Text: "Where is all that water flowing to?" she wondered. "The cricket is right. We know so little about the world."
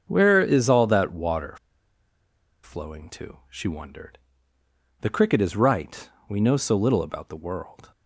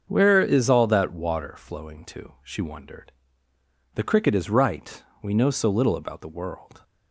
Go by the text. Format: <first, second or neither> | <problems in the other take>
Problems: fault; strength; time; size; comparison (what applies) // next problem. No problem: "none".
second | starts louder than the rest; until 1.0 s; 6.5 dB; also in the second // pauses between "water" and "flowing"; at 1.5 s; 1.0 s long